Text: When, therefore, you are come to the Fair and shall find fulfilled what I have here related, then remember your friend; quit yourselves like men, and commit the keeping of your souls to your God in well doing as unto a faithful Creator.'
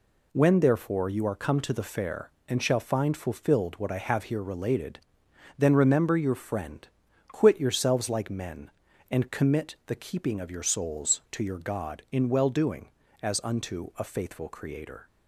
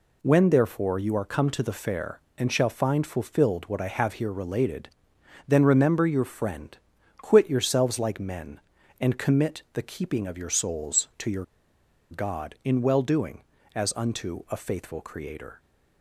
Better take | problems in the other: first | pauses between "your" and "God"; noticeable; at 11.4 s; 0.66 s long

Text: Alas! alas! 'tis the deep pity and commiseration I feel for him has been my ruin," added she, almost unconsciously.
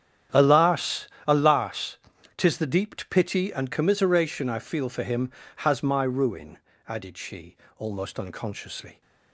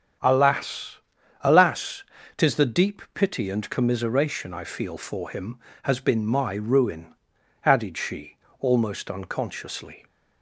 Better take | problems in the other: second | starts louder than the rest; strong; until 1.5 s; 10 dB; strong in the second // skips "been"; at 5.8 s

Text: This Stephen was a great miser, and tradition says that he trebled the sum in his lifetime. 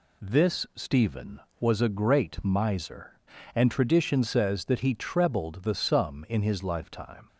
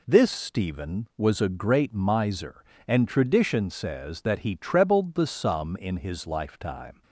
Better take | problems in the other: neither | none

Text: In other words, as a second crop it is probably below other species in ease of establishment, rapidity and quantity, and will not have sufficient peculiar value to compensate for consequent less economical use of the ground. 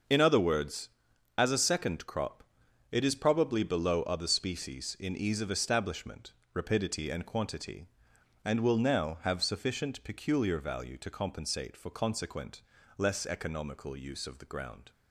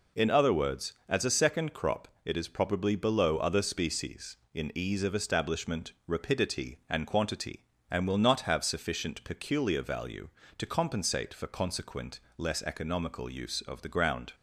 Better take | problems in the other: second | starts louder than the rest; noticeable; until 1.5 s; 6 dB // pauses between "crop" and "it"; noticeable; at 2.4 s; 0.48 s long; slight in the second // says "now" for "not"; at 8.7 s // pauses between "consequent" and "less"; at 12.6 s; 0.38 s long; slight in the second

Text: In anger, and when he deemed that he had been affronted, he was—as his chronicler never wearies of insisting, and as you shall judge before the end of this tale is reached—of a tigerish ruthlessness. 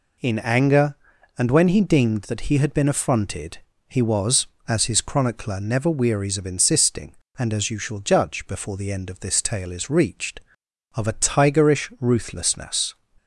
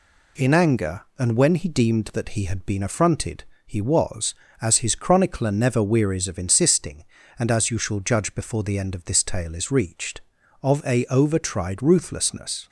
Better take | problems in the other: first | says "overtried" for "tigerish"; at 11.0 s

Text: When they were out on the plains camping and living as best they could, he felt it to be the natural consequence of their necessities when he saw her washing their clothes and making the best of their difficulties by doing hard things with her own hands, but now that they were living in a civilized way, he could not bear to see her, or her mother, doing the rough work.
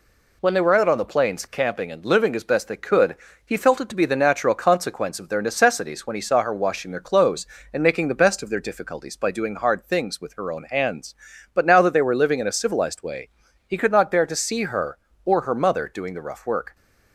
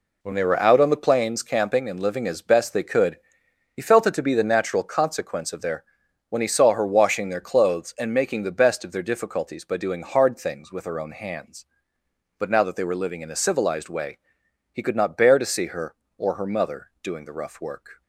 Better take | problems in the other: first | skips "necessities"; at 6.0 s

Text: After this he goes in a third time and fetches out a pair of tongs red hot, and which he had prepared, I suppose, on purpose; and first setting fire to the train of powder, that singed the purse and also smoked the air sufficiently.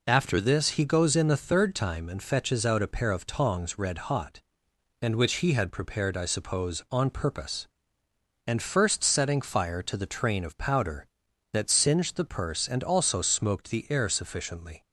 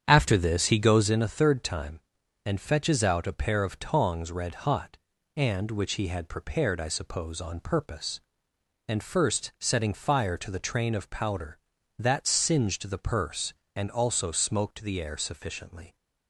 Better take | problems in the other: first | starts louder than the rest; strong; until 1.2 s; 8.5 dB

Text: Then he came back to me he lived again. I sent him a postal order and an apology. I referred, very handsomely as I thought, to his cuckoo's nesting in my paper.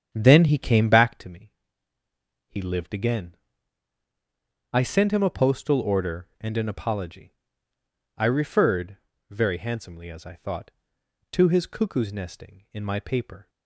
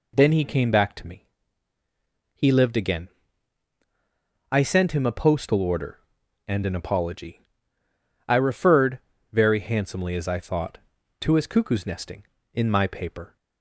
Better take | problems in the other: second | starts louder than the rest; strong; until 1.3 s; 9 dB // pauses between "me" and "he"; at 1.5 s; 1.0 s long; also in the second

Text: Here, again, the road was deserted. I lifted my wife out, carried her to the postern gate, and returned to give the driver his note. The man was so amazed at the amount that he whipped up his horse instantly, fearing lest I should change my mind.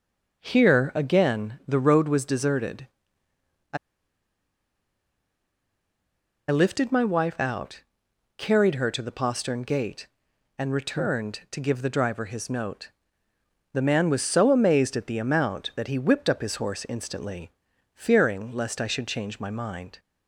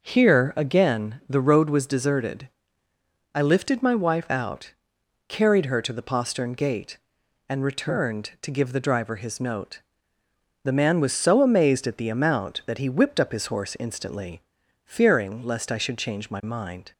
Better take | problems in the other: second | pauses between "I" and "lifted"; strong; at 3.7 s; 2.7 s long

